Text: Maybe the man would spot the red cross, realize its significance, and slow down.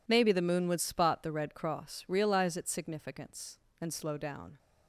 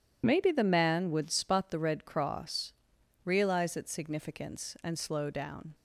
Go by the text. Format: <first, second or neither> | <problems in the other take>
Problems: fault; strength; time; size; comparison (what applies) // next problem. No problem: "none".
second | says "moon" for "man"; at 0.4 s